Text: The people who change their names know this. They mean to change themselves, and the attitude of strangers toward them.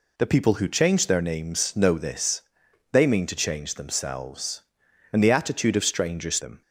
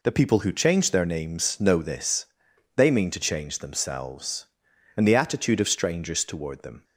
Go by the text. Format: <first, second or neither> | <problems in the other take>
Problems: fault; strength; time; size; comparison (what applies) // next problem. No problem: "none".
second | skips "toward"; at 6.3 s